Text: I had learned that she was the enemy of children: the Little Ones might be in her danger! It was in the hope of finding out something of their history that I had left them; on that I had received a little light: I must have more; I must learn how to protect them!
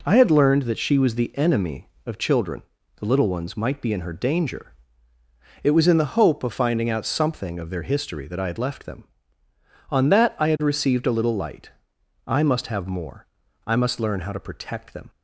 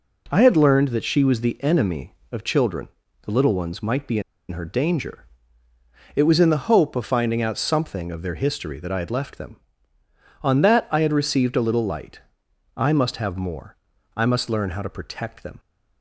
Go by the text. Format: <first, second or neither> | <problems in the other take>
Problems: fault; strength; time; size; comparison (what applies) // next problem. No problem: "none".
first | pauses between "in" and "her"; slight; at 4.2 s; 0.29 s long